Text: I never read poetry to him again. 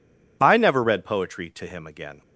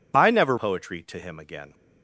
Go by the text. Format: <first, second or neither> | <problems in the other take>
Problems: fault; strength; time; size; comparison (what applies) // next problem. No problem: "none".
first | skips "read"; at 0.5 s